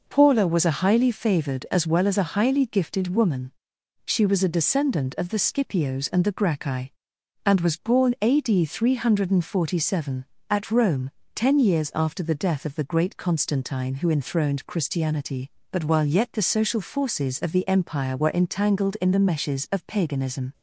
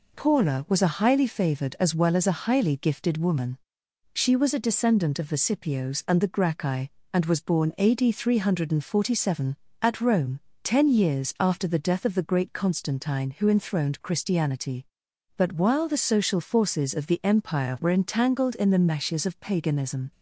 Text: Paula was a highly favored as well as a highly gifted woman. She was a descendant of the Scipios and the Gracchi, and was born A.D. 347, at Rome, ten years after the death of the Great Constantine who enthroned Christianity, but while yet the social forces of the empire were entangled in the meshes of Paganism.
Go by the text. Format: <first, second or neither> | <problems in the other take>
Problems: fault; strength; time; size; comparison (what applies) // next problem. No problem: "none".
first | skips "yet"; at 15.8 s